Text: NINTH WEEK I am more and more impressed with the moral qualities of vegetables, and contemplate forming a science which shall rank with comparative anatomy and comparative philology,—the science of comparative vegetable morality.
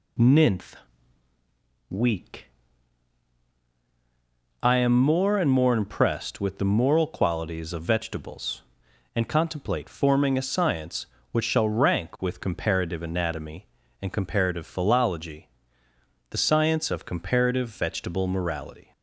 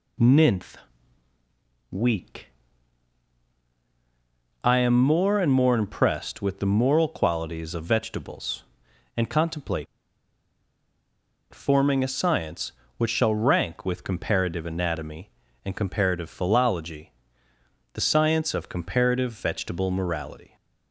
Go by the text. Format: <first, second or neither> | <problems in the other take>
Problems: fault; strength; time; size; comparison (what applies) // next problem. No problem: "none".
first | pauses between "NINTH" and "WEEK"; at 0.7 s; 1.1 s long; also in the first // pauses between "WEEK" and "I"; strong; at 2.4 s; 2.1 s long; strong in the first // pauses between "contemplate" and "forming"; strong; at 9.8 s; 1.6 s long